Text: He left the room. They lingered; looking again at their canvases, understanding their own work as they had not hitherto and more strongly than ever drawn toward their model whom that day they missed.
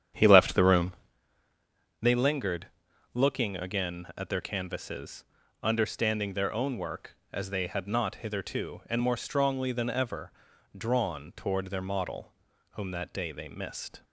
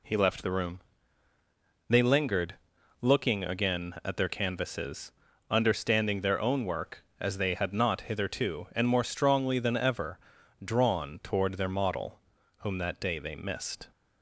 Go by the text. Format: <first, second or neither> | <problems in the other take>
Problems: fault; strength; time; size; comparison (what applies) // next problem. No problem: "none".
second | starts louder than the rest; strong; until 1.2 s; 9 dB // pauses between "ever" and "drawn"; at 10.3 s; 0.44 s long; also in the second // pauses between "model" and "whom"; at 12.3 s; 0.40 s long; also in the second